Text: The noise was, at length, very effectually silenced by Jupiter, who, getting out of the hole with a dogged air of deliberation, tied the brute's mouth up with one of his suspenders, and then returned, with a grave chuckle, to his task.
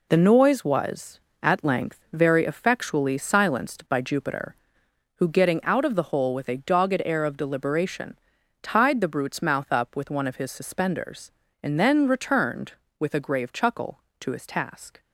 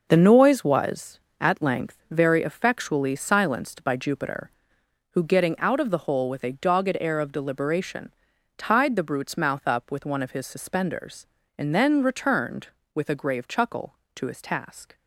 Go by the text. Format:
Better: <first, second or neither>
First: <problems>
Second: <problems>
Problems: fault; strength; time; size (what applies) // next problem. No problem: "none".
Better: first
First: none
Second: starts louder than the rest; noticeable; until 1.1 s; 6 dB